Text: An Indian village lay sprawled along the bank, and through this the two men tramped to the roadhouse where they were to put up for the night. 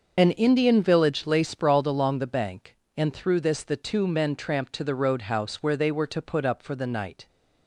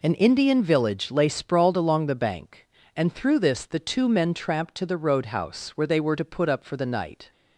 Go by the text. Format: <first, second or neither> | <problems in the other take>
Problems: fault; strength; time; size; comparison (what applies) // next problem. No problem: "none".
second | loses the start of "An"; at 0.1 s; 40 ms // starts louder than the rest; until 1.1 s; 6.5 dB